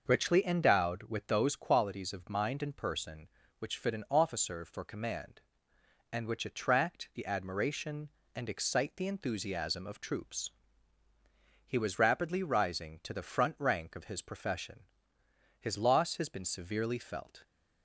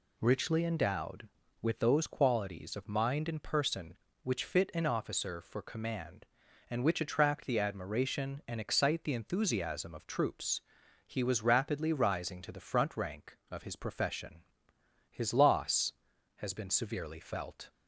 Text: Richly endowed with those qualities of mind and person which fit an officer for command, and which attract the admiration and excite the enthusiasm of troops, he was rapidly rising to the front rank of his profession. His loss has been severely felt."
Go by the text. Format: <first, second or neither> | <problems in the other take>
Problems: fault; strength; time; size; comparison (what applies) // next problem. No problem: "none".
neither | none